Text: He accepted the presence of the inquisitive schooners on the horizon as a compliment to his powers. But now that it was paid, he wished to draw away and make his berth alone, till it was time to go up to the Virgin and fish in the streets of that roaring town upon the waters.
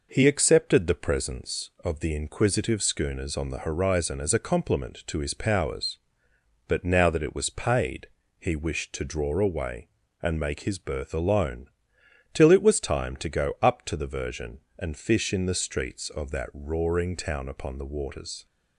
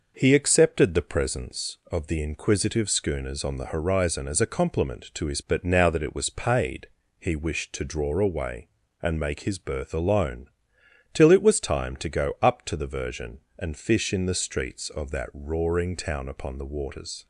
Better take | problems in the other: first | skips "powers"; at 5.4 s

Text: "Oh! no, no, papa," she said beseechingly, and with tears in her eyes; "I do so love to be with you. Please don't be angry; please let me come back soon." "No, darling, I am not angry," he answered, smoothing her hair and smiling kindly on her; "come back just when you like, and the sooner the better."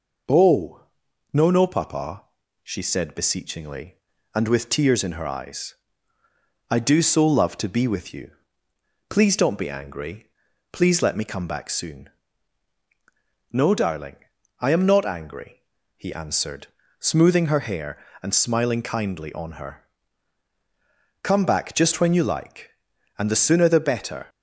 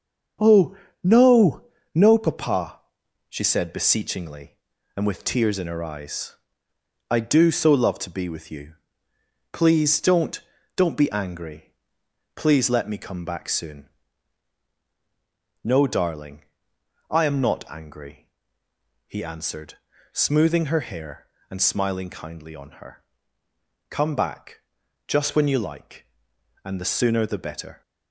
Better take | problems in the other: first | starts louder than the rest; until 1.9 s; 6.5 dB // says "don't" twice; at 10.7 s // pauses between "back" and "just"; at 24.6 s; 0.44 s long

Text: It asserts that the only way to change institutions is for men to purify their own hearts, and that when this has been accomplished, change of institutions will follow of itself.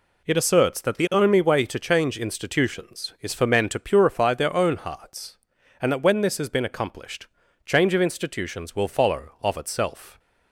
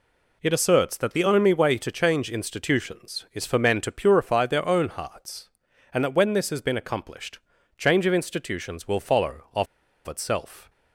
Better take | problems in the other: first | pauses between "of" and "itself"; at 9.6 s; 0.41 s long

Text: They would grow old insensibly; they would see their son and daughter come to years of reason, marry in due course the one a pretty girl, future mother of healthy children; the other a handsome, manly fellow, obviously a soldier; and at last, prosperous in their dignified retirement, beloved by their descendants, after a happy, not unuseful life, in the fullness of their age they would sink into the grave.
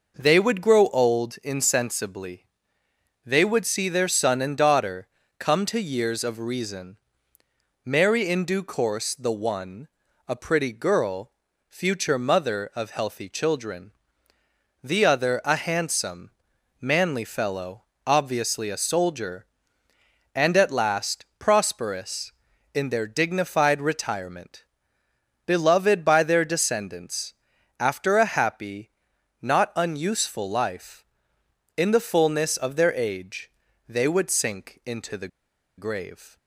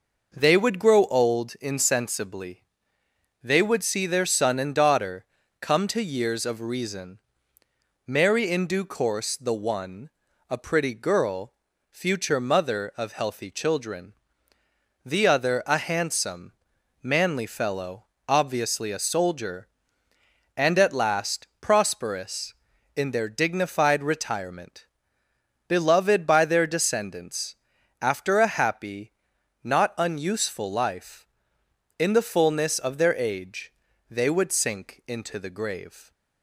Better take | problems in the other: second | pauses between "daughter" and "come"; slight; at 5.0 s; 0.32 s long; also in the second // pauses between "one" and "a"; at 9.8 s; 0.40 s long; also in the second // pauses between "age" and "they"; at 33.5 s; 0.38 s long; also in the second // pauses between "the" and "grave"; noticeable; at 35.2 s; 0.50 s long

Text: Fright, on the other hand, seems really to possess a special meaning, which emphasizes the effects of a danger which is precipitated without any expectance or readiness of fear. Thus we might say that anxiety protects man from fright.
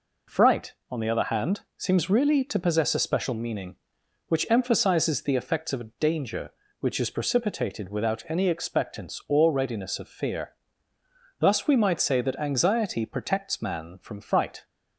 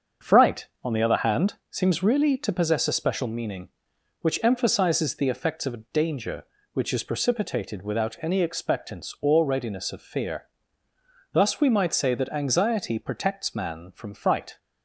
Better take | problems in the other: first | starts louder than the rest; until 1.7 s; 6.5 dB

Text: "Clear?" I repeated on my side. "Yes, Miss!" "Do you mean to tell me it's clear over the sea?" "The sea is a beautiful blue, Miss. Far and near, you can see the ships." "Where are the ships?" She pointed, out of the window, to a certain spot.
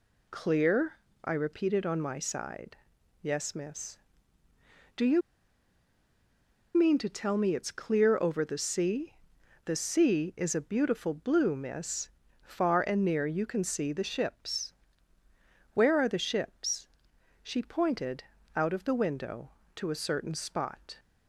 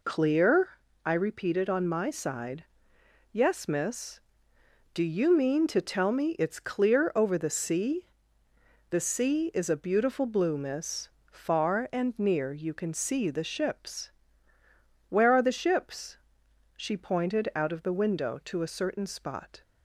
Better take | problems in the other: second | pauses between "you" and "mean"; strong; at 5.2 s; 1.5 s long

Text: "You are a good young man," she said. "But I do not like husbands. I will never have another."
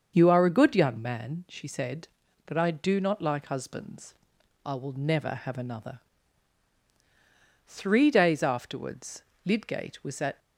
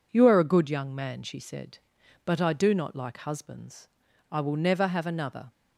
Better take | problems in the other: second | starts louder than the rest; until 1.1 s; 6.5 dB // goes on to say "Three days afterwards Lydgate was at"; strong; from 7.6 s on; 2.7 s long

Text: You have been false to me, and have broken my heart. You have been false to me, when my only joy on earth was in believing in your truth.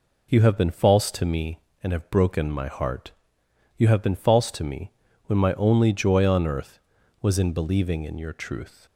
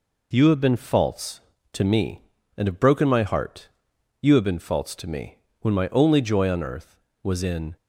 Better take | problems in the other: first | stops before "believing in your truth"; at 7.7 s

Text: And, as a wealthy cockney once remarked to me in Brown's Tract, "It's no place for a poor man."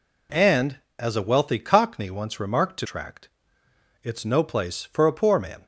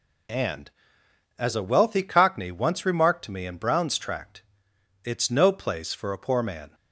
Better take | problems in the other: second | skips "me in Brown's"; at 2.8 s

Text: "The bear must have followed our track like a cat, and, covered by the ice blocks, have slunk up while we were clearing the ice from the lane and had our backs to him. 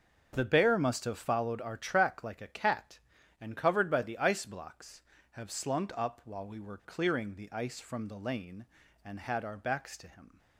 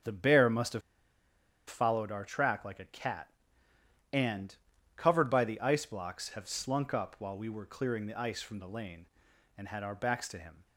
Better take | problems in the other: first | starts louder than the rest; strong; until 1.9 s; 7.5 dB; also in the first // pauses between "have" and "followed"; noticeable; at 0.8 s; 0.87 s long

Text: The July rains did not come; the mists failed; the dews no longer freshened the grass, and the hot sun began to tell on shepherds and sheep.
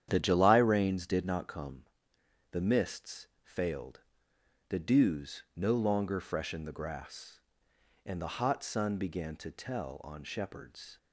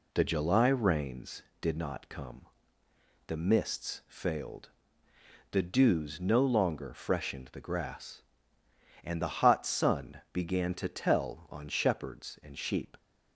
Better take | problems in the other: second | starts louder than the rest; strong; until 1.1 s; 9.5 dB // pauses between "mists" and "failed"; slight; at 3.2 s; 0.16 s long // stops before "and sheep"; at 10.9 s

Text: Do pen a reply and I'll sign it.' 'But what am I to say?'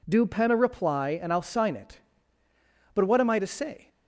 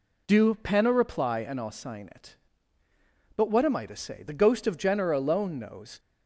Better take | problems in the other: first | goes on to say "The ghost of Jenner alone knows"; strong; from 4.2 s on; 1.7 s long

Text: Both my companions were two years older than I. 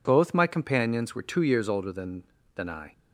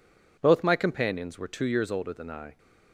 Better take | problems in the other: second | says "than" twice; at 2.5 s

